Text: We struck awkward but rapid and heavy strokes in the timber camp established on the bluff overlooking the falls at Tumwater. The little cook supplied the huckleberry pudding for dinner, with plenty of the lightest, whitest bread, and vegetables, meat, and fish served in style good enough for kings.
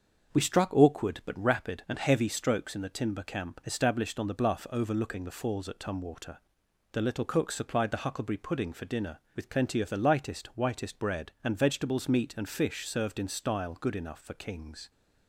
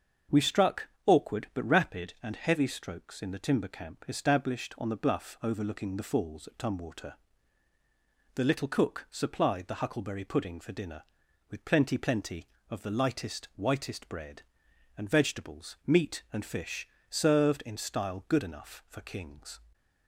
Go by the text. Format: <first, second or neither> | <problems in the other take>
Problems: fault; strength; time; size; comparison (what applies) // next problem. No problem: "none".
first | starts louder than the rest; until 1.5 s; 7 dB; also in the first // pauses between "struck" and "awkward"; slight; at 0.8 s; 0.18 s long // says "plenty" twice; at 11.9 s // pauses between "fish" and "served"; slight; at 16.8 s; 0.24 s long